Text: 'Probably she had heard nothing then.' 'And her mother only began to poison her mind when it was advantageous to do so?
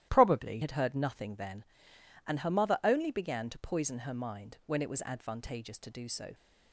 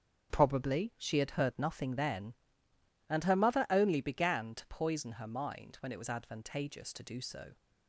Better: second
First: starts louder than the rest; strong; until 1.1 s; 13 dB // skips "she"; at 0.6 s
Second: starts louder than the rest; until 1.3 s; 7 dB

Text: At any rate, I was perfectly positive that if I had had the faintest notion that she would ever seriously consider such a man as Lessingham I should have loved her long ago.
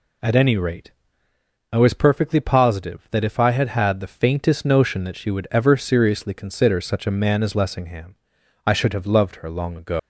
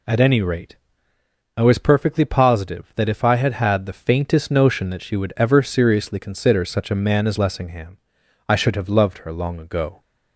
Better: second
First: pauses between "Lessingham" and "I"; noticeable; at 8.1 s; 0.50 s long // leaves "ago" unfinished; at 9.9 s; 175 ms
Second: pauses between "Lessingham" and "I"; noticeable; at 7.9 s; 0.50 s long

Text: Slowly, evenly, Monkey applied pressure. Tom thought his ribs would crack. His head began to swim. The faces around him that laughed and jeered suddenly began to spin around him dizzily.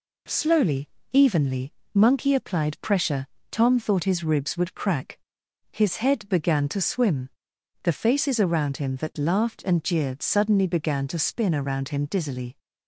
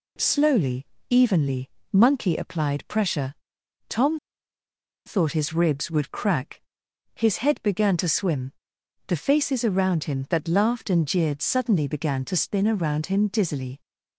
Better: first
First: none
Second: pauses between "Tom" and "thought"; noticeable; at 4.1 s; 0.88 s long

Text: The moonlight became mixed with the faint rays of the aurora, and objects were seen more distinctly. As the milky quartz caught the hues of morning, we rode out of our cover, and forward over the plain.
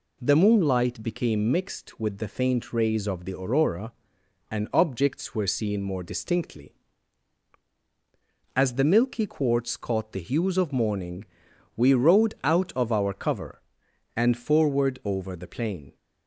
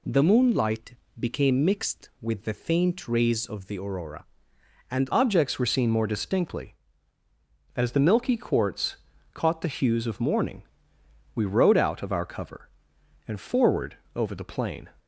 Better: first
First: none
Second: pauses between "moonlight" and "became"; slight; at 0.9 s; 0.24 s long // changes voice at "objects"; from 5.1 s on; 9.7 s long // pauses between "quartz" and "caught"; slight; at 8.9 s; 0.36 s long // pauses between "forward" and "over"; slight; at 13.9 s; 0.18 s long

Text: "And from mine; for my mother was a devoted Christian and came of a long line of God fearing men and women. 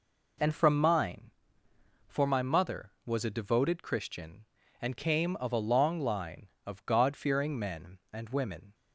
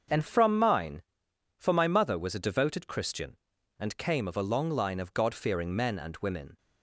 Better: first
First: none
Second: starts louder than the rest; until 1.6 s; 6 dB // changes voice at "from"; from 0.2 s on; 6.3 s long

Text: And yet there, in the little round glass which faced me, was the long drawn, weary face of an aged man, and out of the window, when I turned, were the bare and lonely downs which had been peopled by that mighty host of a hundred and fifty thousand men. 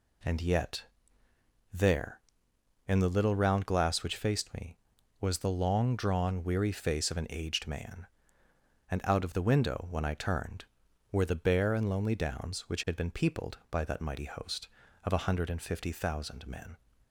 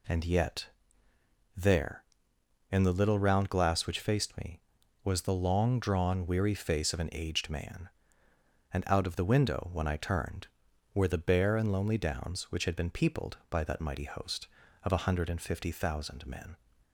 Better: neither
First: pauses between "yet" and "there"; noticeable; at 0.8 s; 0.88 s long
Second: pauses between "yet" and "there"; noticeable; at 0.6 s; 0.88 s long

